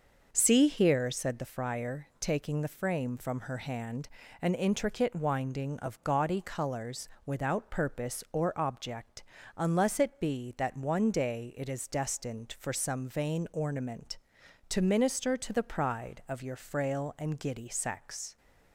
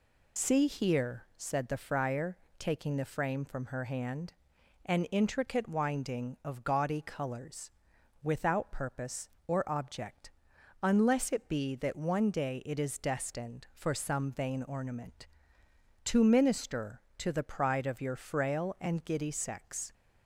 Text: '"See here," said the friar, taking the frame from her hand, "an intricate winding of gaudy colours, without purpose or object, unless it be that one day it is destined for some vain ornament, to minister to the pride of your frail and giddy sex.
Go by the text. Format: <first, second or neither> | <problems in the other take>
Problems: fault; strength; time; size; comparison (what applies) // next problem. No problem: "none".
first | loses the start of "See"; at 0.3 s; 50 ms